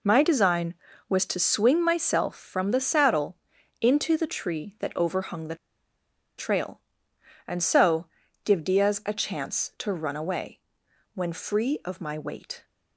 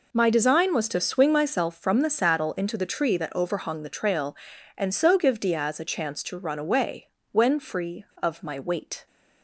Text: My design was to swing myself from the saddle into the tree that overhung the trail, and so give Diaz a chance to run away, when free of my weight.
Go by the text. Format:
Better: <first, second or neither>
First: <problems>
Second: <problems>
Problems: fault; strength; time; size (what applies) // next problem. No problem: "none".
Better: second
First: pauses between "saddle" and "into"; noticeable; at 3.3 s; 0.46 s long // pauses between "the" and "trail"; noticeable; at 5.5 s; 0.83 s long // pauses between "so" and "give"; at 8.0 s; 0.38 s long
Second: none